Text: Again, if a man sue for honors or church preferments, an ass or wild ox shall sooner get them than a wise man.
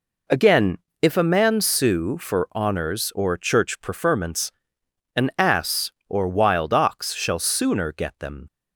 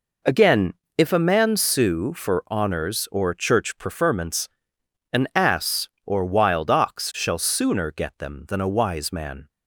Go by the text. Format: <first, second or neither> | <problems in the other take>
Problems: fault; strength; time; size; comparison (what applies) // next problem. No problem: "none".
second | stops before "than a wise man"; at 8.4 s